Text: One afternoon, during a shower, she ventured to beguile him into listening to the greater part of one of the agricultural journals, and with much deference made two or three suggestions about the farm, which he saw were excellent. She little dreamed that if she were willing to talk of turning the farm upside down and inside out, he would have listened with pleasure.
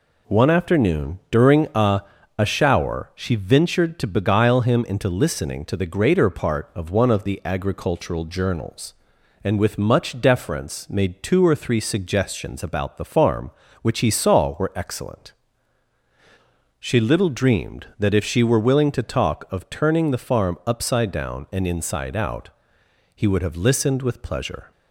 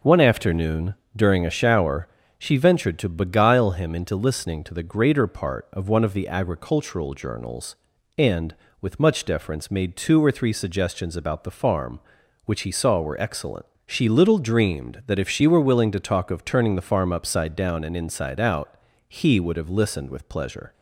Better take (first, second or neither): second